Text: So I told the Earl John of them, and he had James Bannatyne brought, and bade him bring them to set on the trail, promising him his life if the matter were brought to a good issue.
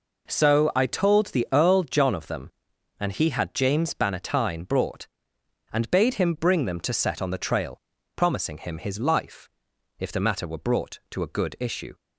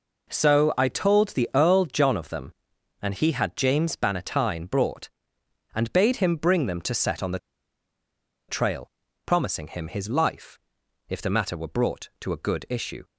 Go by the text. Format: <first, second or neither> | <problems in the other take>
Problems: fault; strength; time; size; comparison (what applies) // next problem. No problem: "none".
first | pauses between "the" and "trail"; at 7.3 s; 1.1 s long // pauses between "life" and "if"; noticeable; at 10.5 s; 0.50 s long; noticeable in the first